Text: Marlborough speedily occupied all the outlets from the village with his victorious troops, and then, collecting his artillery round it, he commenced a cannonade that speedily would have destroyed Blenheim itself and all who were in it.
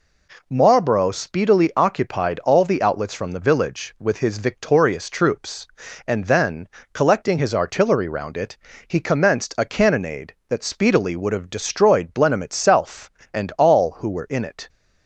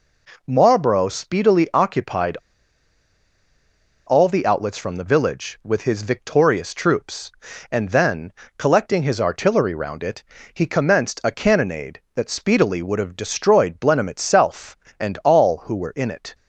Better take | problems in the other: first | pauses between "occupied" and "all"; strong; at 2.3 s; 1.7 s long

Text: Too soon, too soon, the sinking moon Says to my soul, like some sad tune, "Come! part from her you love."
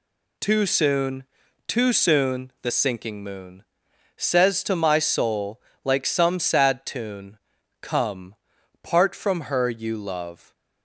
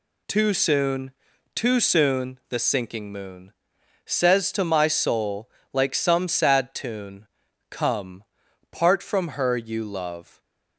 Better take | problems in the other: neither | pauses between "moon" and "Says"; noticeable; the same in both

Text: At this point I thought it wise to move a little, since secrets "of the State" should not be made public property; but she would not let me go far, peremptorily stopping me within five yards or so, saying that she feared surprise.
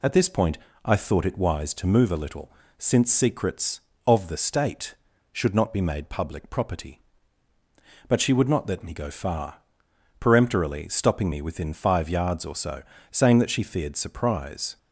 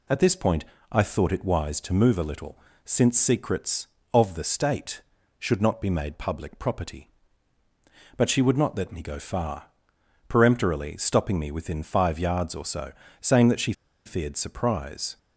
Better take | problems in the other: first | pauses between "point" and "I"; slight; at 0.6 s; 0.26 s long; slight in the first // pauses between "she" and "feared"; slight; at 13.7 s; 0.32 s long

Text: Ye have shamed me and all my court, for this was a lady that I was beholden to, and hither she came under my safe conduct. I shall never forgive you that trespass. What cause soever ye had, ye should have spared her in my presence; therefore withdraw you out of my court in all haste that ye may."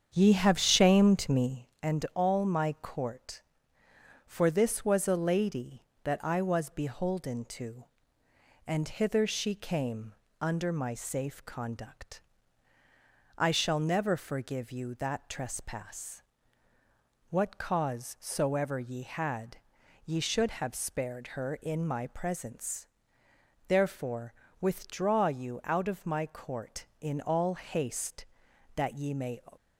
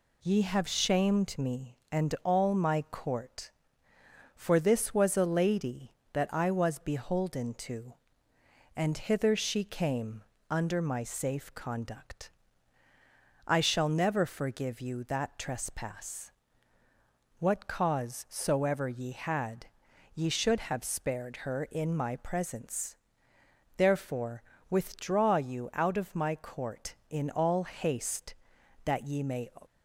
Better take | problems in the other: second | starts louder than the rest; strong; until 1.8 s; 8 dB // pauses between "came" and "under"; slight; at 10.1 s; 0.26 s long; slight in the second // pauses between "therefore" and "withdraw"; slight; at 24.3 s; 0.26 s long; slight in the second

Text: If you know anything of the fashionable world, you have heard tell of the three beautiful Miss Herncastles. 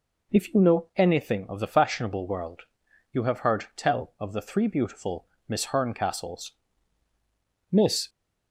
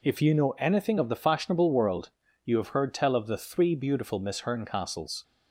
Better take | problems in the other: second | pauses between "beautiful" and "Miss"; slight; at 5.2 s; 0.22 s long // goes on to say "Miss"; slight; from 7.7 s on; 0.38 s long

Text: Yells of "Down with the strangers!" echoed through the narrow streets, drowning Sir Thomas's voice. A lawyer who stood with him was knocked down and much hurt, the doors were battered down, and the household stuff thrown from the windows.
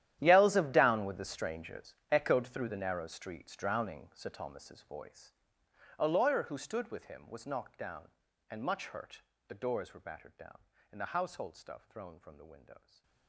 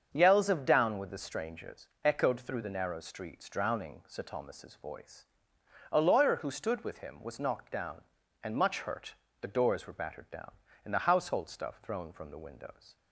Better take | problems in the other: second | gets quieter; strong; throughout; 17.5 dB // starts louder than the rest; strong; until 1.2 s; 11.5 dB; also in the second // stays silent after the last word; slight; from 12.7 s on; 0.5 s long

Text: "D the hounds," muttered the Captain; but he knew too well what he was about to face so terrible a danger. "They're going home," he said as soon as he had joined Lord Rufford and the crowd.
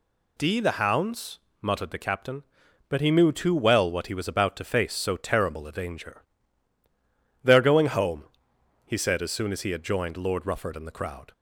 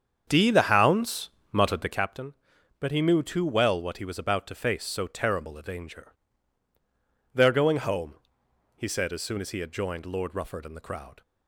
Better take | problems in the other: first | starts louder than the rest; strong; until 2.2 s; 7.5 dB

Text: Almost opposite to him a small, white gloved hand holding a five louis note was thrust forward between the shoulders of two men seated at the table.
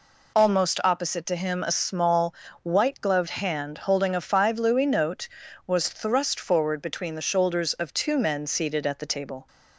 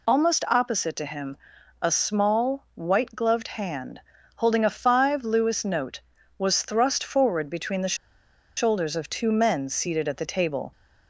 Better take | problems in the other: first | pauses between "him" and "a"; at 1.3 s; 0.42 s long // pauses between "hand" and "holding"; slight; at 3.9 s; 0.36 s long // pauses between "the" and "shoulders"; noticeable; at 7.9 s; 0.61 s long

